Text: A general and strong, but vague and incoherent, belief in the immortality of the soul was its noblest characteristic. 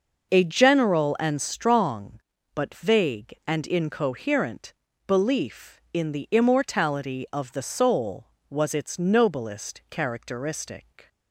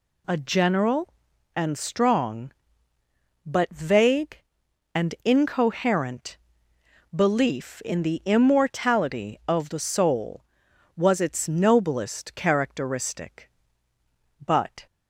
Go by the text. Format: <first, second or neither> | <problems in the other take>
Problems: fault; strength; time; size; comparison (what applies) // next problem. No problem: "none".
first | goes on to say "But"; slight; from 14.4 s on; 0.42 s long